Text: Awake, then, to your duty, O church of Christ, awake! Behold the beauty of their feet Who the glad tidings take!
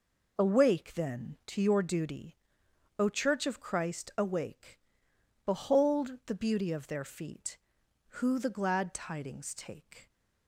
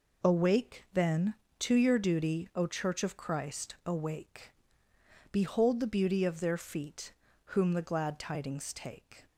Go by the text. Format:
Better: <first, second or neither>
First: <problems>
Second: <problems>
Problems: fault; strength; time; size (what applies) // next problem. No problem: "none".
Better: first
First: none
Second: says "Whom" for "Who"; at 7.4 s